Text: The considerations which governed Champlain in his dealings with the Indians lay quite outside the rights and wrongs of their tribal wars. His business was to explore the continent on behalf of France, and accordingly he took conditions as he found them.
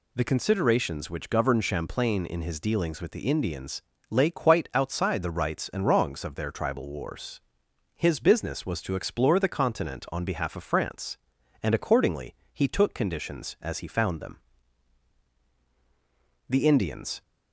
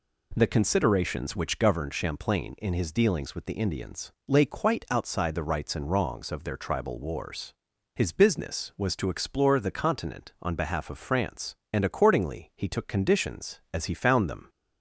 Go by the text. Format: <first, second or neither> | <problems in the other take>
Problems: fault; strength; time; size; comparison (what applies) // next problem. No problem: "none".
second | pauses between "Indians" and "lay"; slight; at 3.8 s; 0.26 s long // pauses between "accordingly" and "he"; slight; at 12.3 s; 0.18 s long // goes on to say "The Indians"; noticeable; from 16.4 s on; 0.72 s long